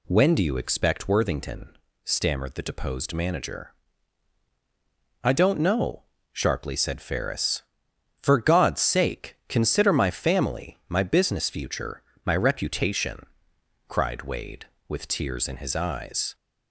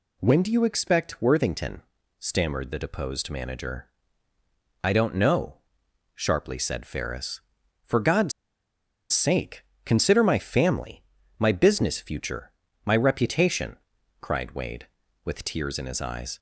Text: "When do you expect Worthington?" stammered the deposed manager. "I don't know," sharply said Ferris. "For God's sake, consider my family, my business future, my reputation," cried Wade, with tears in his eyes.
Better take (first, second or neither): first